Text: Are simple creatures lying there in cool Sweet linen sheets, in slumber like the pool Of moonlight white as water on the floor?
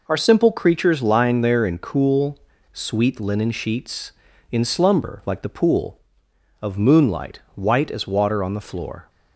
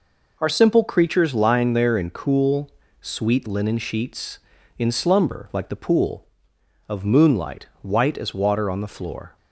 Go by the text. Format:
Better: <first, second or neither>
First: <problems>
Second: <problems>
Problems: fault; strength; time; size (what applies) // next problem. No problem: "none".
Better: neither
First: pauses between "cool" and "Sweet"; slight; at 2.3 s; 0.33 s long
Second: pauses between "cool" and "Sweet"; slight; at 2.6 s; 0.30 s long